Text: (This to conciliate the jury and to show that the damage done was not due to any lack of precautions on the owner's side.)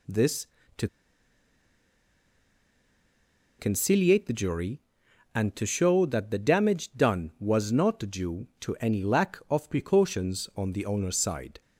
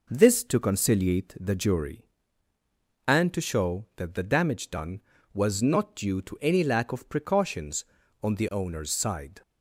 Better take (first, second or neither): second